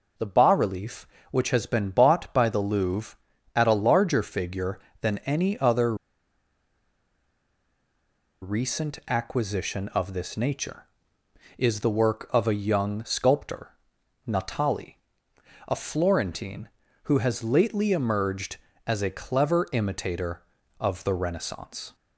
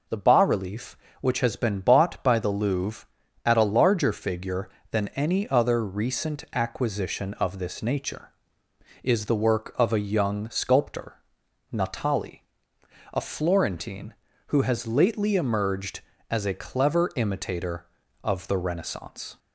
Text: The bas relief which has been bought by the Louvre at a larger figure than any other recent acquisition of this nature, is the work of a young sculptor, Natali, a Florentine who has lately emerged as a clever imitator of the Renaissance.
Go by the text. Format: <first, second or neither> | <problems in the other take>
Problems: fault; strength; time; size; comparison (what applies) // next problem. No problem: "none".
second | pauses between "other" and "recent"; strong; at 5.9 s; 2.4 s long